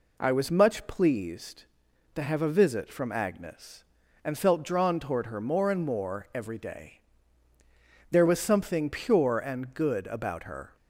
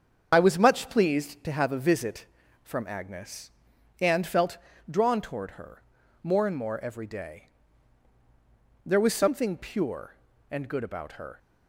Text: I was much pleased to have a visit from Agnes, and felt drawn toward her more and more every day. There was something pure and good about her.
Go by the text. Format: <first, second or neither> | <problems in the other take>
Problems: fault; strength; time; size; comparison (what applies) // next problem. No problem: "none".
first | loses the start of "I"; at 0.3 s; 55 ms // starts louder than the rest; until 1.3 s; 7 dB // pauses between "felt" and "drawn"; slight; at 4.5 s; 0.32 s long // pauses between "her" and "more"; at 5.8 s; 0.40 s long